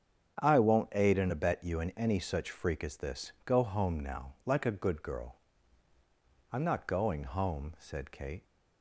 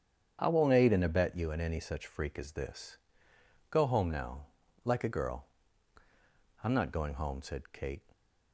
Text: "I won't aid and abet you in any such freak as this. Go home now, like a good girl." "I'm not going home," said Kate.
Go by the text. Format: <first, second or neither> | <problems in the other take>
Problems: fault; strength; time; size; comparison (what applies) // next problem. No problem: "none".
first | starts louder than the rest; strong; until 1.4 s; 8 dB; strong in the first // skips "good"; at 5.1 s